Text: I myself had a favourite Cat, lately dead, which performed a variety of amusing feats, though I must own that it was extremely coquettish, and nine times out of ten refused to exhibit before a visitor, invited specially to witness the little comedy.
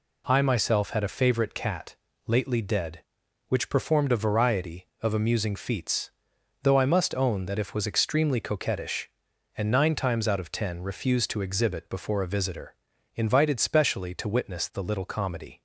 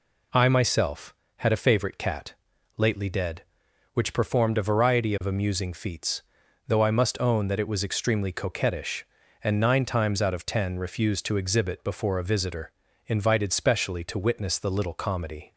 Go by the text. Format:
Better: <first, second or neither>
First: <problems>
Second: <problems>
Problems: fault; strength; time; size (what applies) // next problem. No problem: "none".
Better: second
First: says "if" for "it"; at 7.5 s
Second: none